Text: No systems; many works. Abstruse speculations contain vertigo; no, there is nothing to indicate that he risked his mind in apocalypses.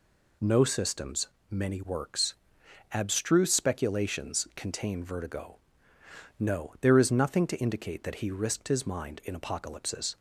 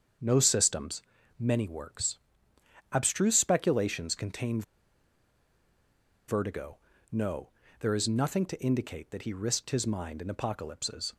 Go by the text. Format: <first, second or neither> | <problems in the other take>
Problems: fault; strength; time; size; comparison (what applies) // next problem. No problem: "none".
first | starts louder than the rest; until 1.5 s; 7 dB // pauses between "contain" and "vertigo"; strong; at 4.6 s; 1.6 s long